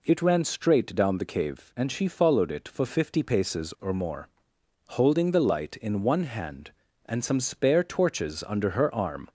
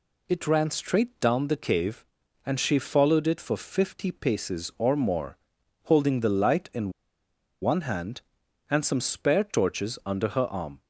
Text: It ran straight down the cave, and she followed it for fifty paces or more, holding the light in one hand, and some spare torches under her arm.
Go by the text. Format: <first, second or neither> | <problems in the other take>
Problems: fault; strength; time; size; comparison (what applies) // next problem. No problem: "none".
first | pauses between "in" and "one"; noticeable; at 6.8 s; 0.72 s long